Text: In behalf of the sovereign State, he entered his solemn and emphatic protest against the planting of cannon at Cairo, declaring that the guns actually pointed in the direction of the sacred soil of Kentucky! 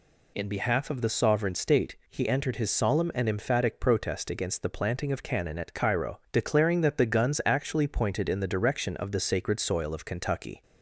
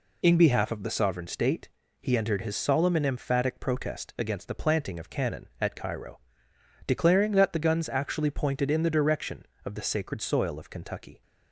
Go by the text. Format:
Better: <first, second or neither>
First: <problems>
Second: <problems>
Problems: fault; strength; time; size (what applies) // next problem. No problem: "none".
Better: neither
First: none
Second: none